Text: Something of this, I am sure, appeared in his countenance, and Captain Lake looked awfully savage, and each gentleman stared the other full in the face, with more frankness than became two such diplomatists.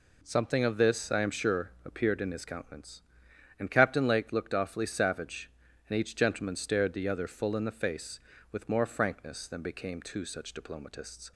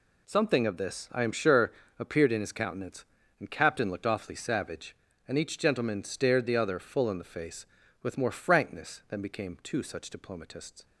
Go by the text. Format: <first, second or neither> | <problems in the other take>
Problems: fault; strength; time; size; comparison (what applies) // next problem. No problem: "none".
first | skips "Lake"; at 3.9 s